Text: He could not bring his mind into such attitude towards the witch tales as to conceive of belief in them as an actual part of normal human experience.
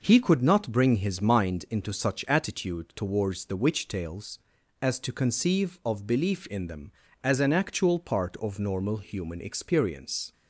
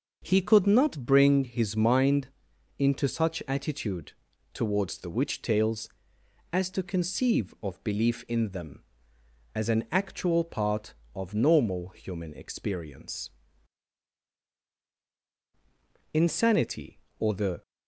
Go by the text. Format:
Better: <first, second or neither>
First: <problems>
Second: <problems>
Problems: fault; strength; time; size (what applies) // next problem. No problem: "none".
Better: first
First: none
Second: starts louder than the rest; noticeable; until 1.2 s; 6 dB // pauses between "mind" and "into"; noticeable; at 2.2 s; 0.50 s long // pauses between "attitude" and "towards"; at 4.1 s; 0.42 s long // goes on to say "Insanity or the"; from 16.1 s on; 1.4 s long